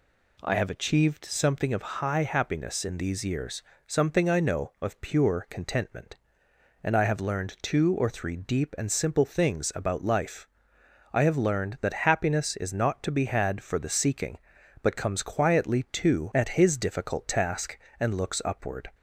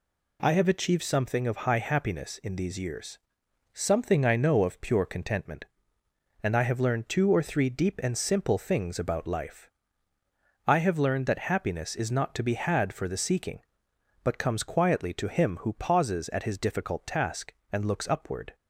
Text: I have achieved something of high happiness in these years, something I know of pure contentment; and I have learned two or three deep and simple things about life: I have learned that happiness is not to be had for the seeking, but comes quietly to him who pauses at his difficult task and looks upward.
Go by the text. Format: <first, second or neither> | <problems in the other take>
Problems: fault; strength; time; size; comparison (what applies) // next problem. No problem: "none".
second | skips "him who pauses"; at 16.3 s